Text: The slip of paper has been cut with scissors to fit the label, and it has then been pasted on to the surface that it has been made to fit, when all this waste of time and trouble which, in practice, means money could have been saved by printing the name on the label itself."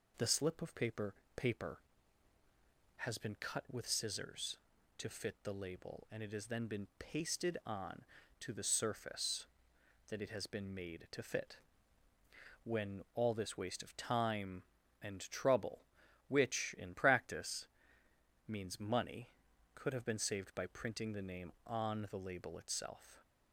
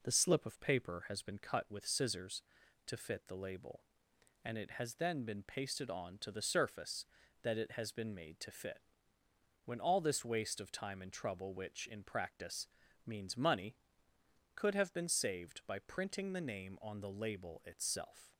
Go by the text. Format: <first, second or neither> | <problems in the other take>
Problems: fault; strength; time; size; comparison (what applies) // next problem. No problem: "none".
second | says "paper" twice; at 1.3 s